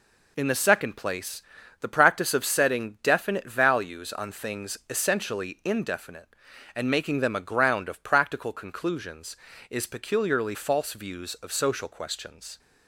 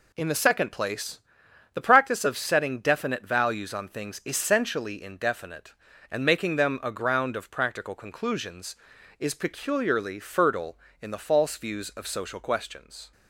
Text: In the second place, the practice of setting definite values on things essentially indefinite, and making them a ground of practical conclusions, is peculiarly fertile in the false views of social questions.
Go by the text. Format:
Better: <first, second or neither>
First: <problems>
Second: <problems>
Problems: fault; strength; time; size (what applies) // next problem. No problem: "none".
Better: second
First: skips "fertile in the"; at 10.5 s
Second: none